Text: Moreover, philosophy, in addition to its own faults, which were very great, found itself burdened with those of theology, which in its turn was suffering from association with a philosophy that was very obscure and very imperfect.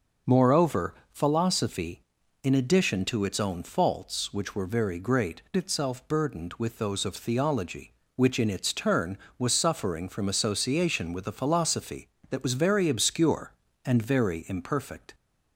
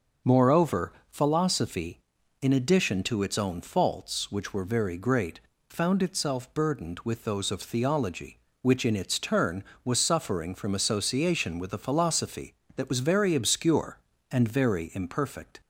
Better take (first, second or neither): second